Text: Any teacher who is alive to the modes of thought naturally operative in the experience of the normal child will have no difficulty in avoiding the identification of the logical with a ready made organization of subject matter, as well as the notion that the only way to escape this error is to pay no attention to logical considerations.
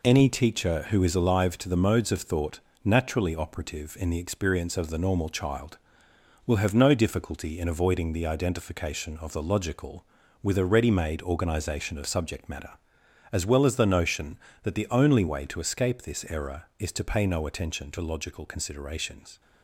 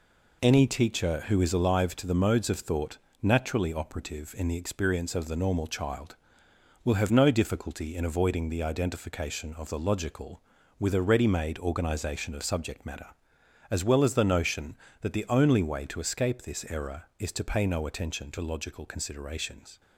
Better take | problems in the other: neither | pauses between "thought" and "naturally"; slight; the same in both

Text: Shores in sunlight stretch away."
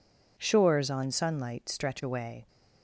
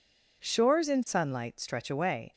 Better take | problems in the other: second | says "on" for "in"; at 0.8 s

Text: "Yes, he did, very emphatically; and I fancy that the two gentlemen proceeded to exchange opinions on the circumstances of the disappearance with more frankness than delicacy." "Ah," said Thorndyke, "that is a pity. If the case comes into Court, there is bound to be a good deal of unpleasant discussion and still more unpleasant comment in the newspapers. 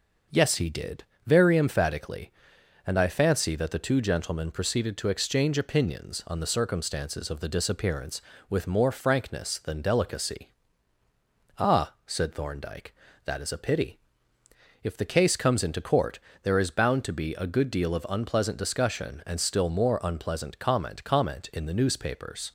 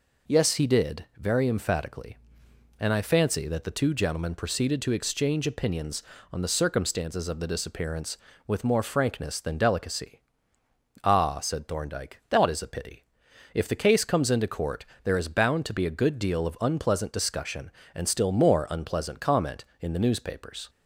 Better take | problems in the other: second | says "comment" twice; at 21.0 s

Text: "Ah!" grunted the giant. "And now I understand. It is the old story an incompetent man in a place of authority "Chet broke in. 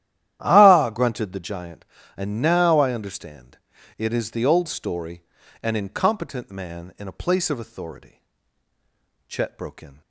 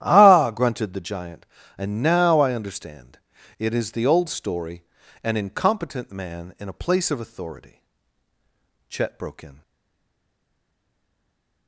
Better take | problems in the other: first | starts louder than the rest; strong; until 1.0 s; 12 dB; strong in the first // pauses between "story" and "an"; at 4.8 s; 0.40 s long; also in the first // pauses between "authority" and "Chet"; at 7.8 s; 1.0 s long; also in the first // stays silent after the last word; noticeable; from 9.6 s on; 2.0 s long

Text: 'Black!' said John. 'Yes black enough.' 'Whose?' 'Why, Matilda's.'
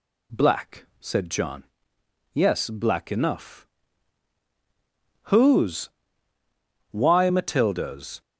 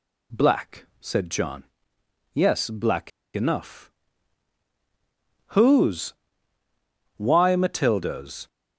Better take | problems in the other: first | pauses between "black" and "enough"; slight; at 3.1 s; 0.24 s long

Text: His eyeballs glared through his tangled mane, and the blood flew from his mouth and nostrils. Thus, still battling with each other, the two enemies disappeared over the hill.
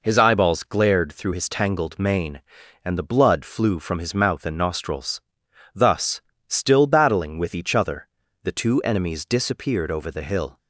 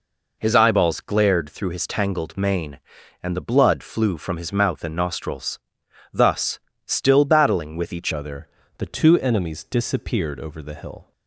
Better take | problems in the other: first | changes voice at "other"; from 8.1 s on; 3.0 s long

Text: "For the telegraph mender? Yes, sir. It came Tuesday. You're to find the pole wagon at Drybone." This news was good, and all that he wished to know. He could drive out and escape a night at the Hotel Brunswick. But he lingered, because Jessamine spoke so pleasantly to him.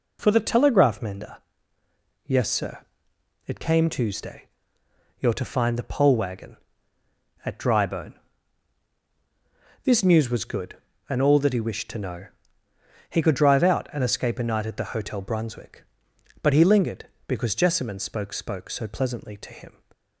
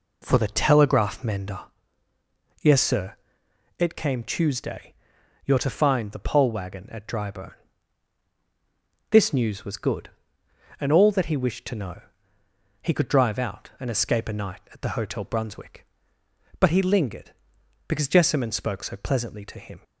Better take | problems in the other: second | says "spoke" twice; at 18.3 s

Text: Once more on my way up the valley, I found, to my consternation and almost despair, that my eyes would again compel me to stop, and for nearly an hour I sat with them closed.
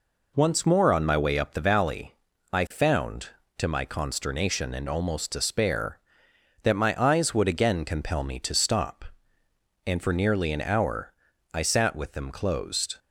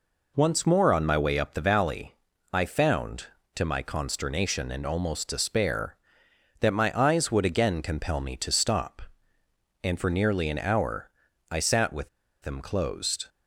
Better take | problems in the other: first | pauses between "hour" and "I"; at 11.0 s; 0.44 s long; also in the first // pauses between "with" and "them"; slight; at 12.0 s; 0.33 s long

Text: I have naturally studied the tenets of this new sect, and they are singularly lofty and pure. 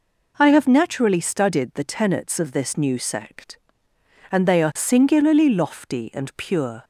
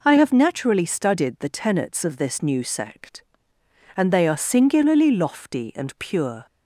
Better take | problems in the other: neither | none

